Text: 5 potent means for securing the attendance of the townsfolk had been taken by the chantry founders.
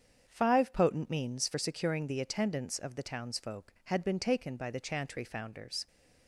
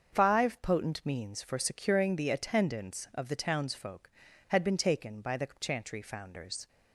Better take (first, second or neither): neither